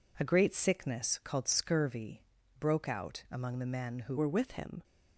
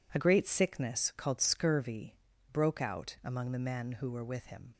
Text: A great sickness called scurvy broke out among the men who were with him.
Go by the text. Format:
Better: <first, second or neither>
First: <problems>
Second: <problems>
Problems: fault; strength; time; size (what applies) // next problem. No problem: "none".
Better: second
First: pauses between "scurvy" and "broke"; slight; at 2.2 s; 0.36 s long // changes voice at "were"; from 4.1 s on; 0.7 s long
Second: pauses between "scurvy" and "broke"; slight; at 2.1 s; 0.36 s long